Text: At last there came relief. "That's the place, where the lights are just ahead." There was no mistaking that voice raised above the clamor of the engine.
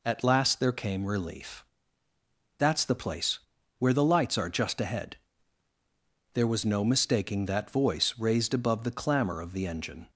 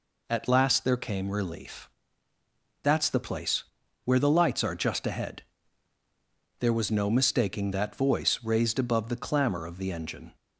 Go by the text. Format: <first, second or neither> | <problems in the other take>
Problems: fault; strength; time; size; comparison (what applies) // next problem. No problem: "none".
neither | none